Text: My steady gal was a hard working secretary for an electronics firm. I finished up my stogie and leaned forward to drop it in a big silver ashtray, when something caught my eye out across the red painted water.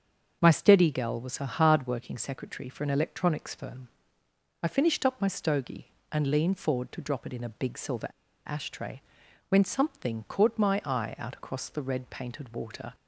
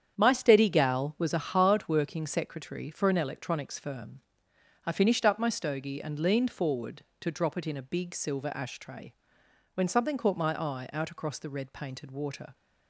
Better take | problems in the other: second | starts louder than the rest; until 1.4 s; 7 dB; strong in the second // pauses between "silver" and "ashtray"; at 8.0 s; 0.39 s long

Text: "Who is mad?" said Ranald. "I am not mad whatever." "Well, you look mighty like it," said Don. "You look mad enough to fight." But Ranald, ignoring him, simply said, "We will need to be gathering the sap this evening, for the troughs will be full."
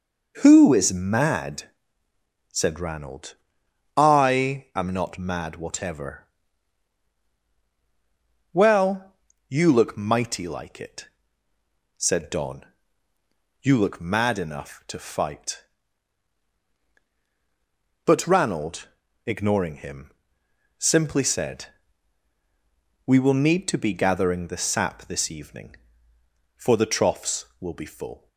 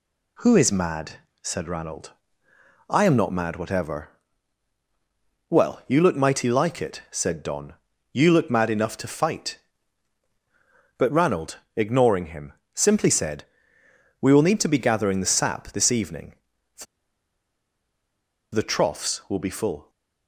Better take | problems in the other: first | pauses between "for" and "the"; strong; at 16.8 s; 1.6 s long

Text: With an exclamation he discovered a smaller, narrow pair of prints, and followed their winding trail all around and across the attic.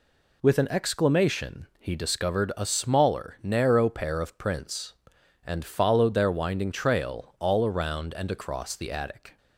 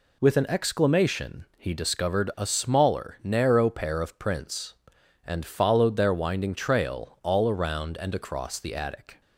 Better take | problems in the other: neither | none

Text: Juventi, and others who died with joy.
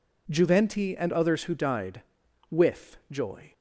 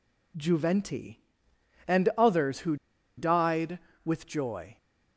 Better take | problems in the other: first | pauses between "who" and "died"; at 2.7 s; 0.42 s long

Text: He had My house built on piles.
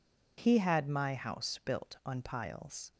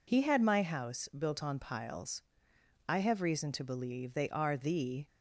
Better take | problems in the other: first | goes on to say "I have reason to believe they are the"; strong; from 2.8 s on; 2.1 s long

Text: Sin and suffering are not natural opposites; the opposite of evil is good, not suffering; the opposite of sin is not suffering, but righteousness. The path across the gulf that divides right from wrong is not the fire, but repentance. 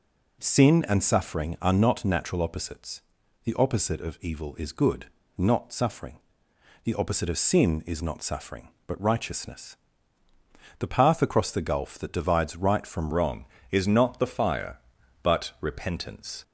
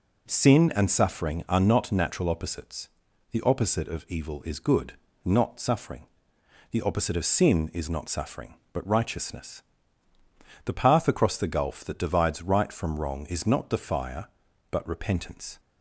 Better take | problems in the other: second | changes voice at "wrong"; from 13.1 s on; 3.3 s long

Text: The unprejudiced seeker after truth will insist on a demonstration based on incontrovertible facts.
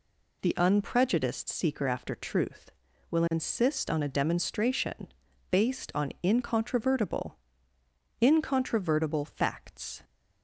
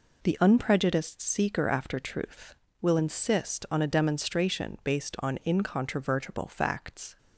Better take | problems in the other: second | pauses between "demonstration" and "based"; at 5.0 s; 0.42 s long // says "incontrovertible" twice; at 8.2 s

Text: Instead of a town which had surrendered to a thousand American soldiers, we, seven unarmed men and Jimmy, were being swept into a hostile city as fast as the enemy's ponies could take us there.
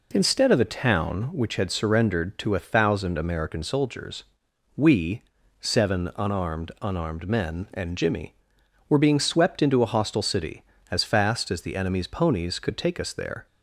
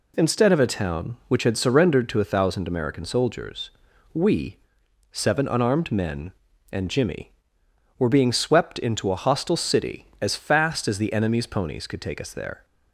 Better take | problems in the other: second | says "unarmed" twice; at 6.8 s

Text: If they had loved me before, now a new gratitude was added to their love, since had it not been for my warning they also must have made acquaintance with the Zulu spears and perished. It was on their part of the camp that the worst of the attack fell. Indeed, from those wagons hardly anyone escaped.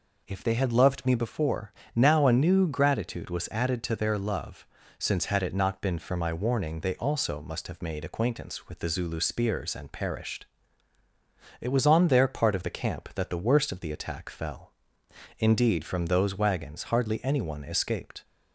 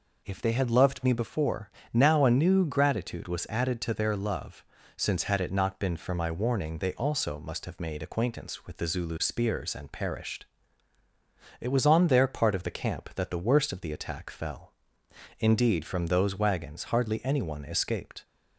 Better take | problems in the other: neither | none

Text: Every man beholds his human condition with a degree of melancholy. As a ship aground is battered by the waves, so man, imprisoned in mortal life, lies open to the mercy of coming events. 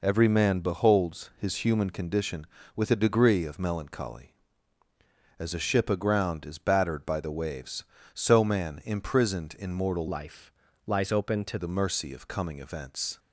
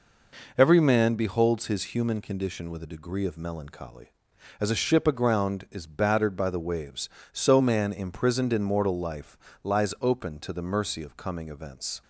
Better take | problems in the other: second | changes voice from "life" to "to"; from 10.0 to 11.5 s; 1.5 s long

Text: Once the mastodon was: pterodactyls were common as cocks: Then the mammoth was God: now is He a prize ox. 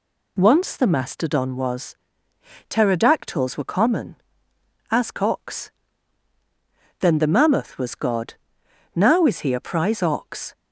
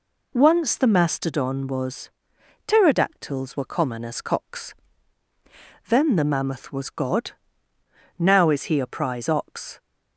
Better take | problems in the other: neither | none

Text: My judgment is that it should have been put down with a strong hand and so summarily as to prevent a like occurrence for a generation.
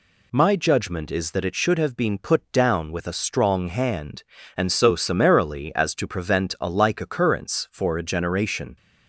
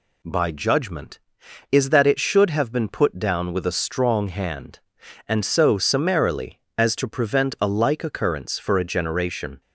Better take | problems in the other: first | says "By" for "My"; at 0.2 s

